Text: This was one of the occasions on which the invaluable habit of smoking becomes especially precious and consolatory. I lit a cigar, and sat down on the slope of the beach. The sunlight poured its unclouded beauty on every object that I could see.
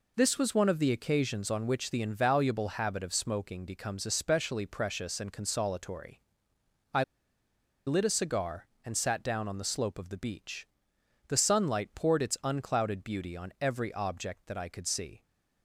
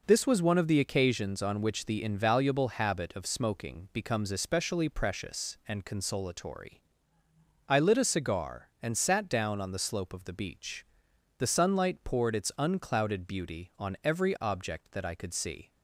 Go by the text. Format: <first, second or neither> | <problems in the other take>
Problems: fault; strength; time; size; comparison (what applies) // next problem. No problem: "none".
second | pauses between "I" and "lit"; noticeable; at 7.0 s; 0.84 s long